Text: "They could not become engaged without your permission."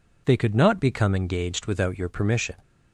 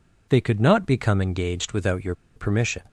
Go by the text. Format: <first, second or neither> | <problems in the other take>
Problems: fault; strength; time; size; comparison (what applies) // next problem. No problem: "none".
first | pauses between "your" and "permission"; slight; at 2.1 s; 0.23 s long